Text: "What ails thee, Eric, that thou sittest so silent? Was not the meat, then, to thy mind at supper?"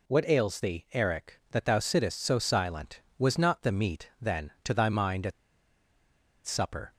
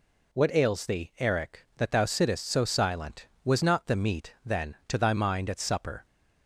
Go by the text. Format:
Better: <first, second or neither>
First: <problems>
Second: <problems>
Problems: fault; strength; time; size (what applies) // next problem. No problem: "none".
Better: second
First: pauses between "at" and "supper"; at 5.3 s; 1.1 s long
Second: none